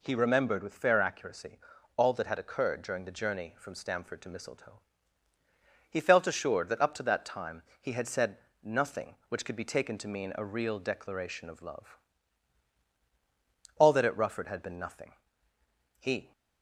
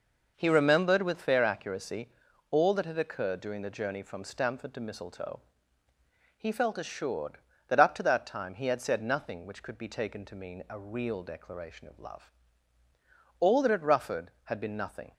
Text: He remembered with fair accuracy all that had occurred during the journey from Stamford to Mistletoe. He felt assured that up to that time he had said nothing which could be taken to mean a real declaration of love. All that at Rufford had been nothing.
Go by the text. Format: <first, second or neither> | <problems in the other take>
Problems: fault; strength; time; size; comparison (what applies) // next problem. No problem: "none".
second | pauses between "accuracy" and "all"; at 1.5 s; 0.38 s long; also in the second // pauses between "time" and "he"; slight; at 7.6 s; 0.18 s long // pauses between "said" and "nothing"; slight; at 8.3 s; 0.26 s long // goes on to say "He"; slight; from 15.9 s on; 0.32 s long